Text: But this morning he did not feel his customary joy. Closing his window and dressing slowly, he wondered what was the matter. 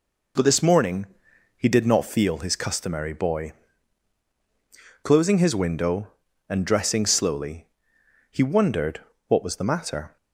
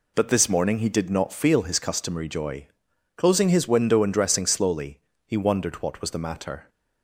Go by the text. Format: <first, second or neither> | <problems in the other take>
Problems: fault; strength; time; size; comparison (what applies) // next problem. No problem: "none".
second | pauses between "morning" and "he"; noticeable; at 1.0 s; 0.50 s long // says "boy" for "joy"; at 3.1 s // pauses between "wondered" and "what"; slight; at 8.9 s; 0.30 s long